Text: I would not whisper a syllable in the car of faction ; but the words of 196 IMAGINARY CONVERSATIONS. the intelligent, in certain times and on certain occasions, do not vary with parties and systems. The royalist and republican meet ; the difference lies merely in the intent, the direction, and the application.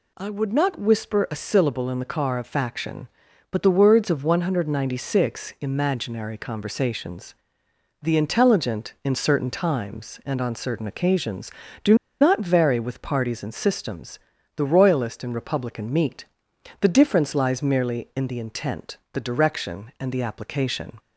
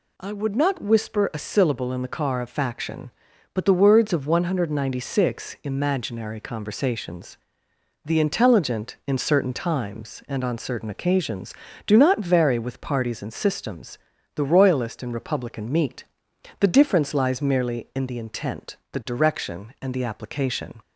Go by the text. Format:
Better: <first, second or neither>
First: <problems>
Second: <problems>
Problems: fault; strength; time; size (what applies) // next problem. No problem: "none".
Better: second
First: pauses between "do" and "not"; slight; at 11.9 s; 0.25 s long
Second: none